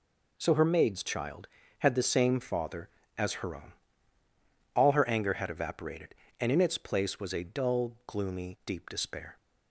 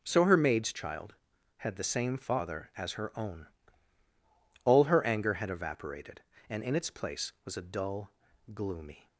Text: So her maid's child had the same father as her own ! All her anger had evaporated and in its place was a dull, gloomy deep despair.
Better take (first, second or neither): first